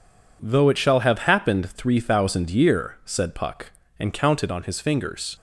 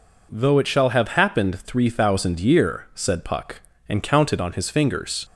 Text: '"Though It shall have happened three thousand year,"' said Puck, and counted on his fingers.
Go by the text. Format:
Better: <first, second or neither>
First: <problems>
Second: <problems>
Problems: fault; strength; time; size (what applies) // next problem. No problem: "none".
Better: second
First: gets quieter; strong; throughout; 8.5 dB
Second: none